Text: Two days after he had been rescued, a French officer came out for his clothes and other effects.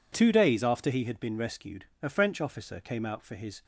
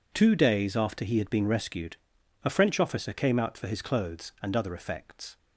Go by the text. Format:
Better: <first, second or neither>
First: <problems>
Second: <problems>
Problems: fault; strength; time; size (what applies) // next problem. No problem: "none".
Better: second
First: stops before "clothes and other effects"; at 3.6 s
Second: none